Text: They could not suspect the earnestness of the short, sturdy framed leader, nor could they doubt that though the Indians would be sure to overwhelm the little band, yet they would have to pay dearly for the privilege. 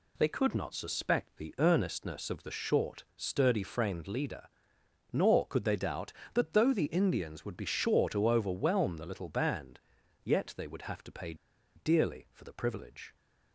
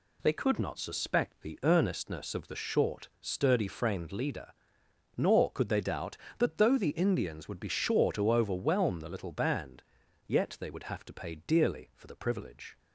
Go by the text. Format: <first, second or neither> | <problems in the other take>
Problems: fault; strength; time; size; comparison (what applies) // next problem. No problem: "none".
second | pauses between "pay" and "dearly"; at 11.3 s; 0.41 s long